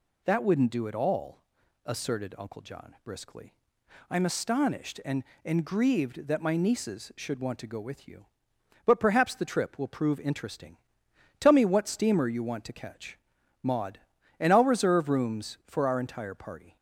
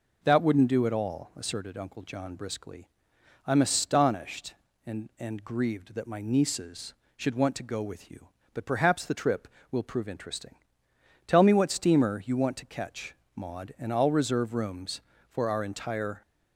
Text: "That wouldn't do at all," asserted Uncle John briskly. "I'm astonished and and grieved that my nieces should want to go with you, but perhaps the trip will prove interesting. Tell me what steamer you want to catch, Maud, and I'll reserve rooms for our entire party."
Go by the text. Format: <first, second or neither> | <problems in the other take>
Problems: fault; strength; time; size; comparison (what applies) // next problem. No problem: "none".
first | stops before "party"; at 16.2 s